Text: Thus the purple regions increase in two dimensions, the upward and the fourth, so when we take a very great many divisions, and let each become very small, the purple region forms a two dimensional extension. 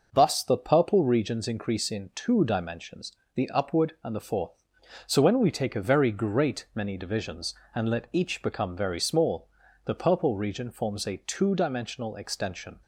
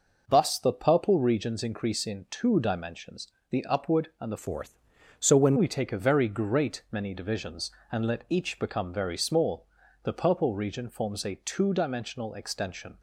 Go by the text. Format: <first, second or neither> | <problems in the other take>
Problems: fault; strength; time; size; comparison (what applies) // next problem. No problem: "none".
first | changes voice from "fourth" to "when"; from 4.3 to 5.5 s; 1.2 s long